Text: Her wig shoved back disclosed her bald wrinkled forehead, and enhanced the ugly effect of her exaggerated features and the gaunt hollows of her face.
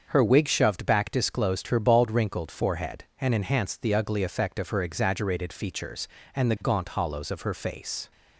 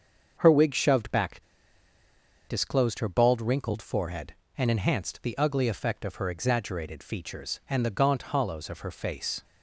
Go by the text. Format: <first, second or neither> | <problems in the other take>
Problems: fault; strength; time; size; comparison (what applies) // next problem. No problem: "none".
first | starts louder than the rest; until 1.3 s; 6.5 dB; also in the first // pauses between "back" and "disclosed"; at 1.4 s; 1.0 s long